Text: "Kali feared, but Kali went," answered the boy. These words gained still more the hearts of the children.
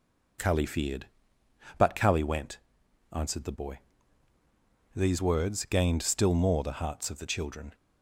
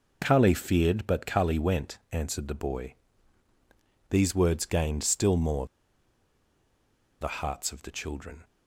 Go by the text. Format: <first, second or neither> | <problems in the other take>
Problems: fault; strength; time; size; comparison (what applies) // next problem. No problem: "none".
first | pauses between "more" and "the"; strong; at 5.6 s; 1.5 s long